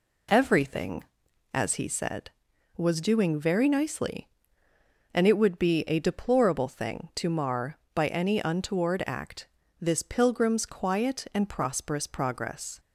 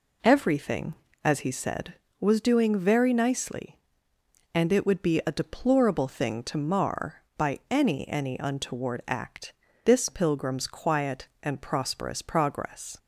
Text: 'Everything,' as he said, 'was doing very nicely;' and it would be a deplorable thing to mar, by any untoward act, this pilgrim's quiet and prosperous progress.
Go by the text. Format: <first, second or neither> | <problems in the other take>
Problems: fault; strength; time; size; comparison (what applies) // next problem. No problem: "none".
first | says "any" twice; at 8.0 s